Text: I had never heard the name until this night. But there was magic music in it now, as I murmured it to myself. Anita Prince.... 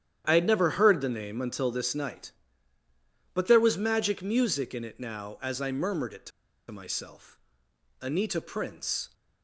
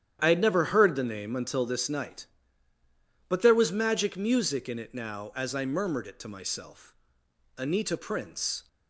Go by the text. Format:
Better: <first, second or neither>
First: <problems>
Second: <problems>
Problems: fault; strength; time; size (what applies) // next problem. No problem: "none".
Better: second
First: starts louder than the rest; strong; until 1.2 s; 9.5 dB // pauses between "to" and "myself"; at 6.3 s; 0.40 s long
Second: starts louder than the rest; strong; until 1.2 s; 9.5 dB